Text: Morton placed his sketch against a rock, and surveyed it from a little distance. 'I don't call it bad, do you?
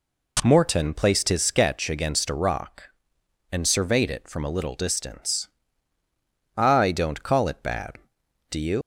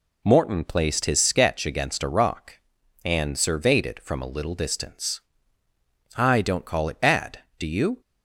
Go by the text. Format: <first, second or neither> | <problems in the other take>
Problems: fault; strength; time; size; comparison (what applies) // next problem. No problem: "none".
second | leaves "you" unfinished; at 8.8 s; 105 ms